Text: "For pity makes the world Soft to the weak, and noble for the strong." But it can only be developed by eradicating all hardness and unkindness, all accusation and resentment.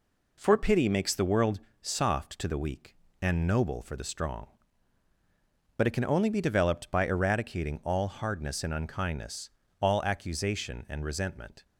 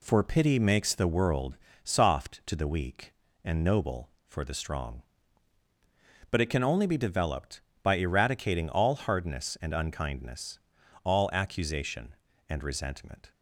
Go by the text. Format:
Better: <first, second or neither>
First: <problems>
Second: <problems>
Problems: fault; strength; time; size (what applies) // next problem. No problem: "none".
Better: neither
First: pauses between "world" and "Soft"; slight; at 1.5 s; 0.22 s long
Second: pauses between "world" and "Soft"; slight; at 1.5 s; 0.30 s long